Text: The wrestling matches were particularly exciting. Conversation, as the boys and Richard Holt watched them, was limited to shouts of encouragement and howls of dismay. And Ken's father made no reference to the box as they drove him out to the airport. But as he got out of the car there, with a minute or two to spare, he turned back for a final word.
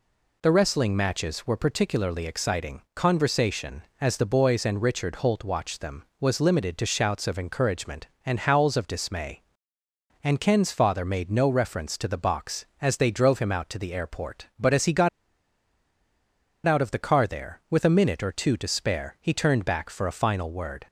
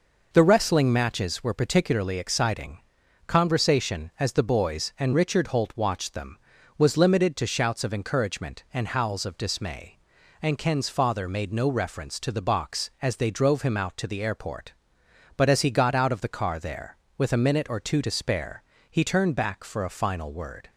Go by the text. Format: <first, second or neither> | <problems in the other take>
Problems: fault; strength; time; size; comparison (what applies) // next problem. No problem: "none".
second | pauses between "got" and "out"; strong; at 15.0 s; 1.5 s long